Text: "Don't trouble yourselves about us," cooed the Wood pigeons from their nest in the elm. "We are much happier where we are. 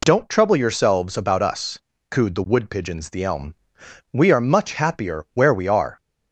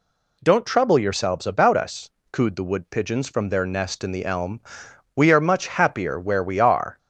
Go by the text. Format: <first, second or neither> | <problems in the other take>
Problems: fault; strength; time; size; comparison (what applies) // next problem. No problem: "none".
second | skips "from their nest in"; at 3.0 s